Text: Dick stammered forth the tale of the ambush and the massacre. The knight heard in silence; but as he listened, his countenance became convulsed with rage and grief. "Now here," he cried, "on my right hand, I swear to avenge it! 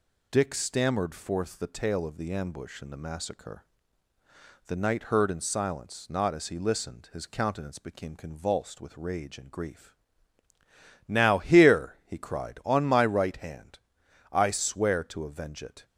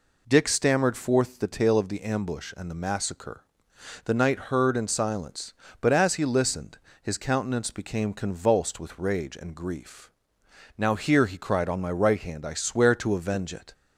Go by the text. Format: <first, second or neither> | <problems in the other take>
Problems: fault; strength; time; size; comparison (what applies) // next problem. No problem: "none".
second | says "not" for "but"; at 6.0 s